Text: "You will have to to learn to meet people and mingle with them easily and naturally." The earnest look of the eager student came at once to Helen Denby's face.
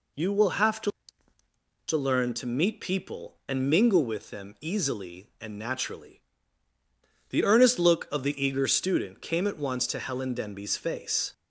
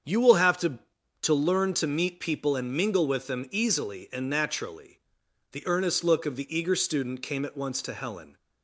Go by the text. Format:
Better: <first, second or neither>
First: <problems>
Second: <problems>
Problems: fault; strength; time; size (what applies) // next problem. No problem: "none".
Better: first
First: none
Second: starts louder than the rest; strong; until 1.5 s; 7.5 dB // stops before "Denby's face"; at 8.3 s